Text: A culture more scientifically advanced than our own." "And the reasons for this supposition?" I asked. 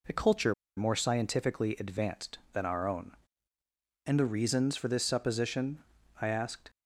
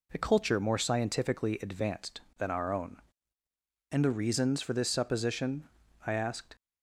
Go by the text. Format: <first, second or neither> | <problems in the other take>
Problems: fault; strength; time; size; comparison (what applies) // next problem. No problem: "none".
second | pauses between "culture" and "more"; slight; at 0.5 s; 0.23 s long